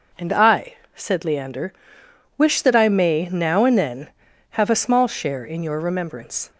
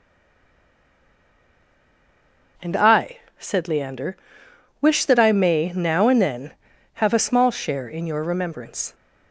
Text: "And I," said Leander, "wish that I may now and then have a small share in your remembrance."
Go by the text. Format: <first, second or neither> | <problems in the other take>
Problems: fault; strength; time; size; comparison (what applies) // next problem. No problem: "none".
first | stays silent before the first word; strong; until 2.5 s; 2.5 s long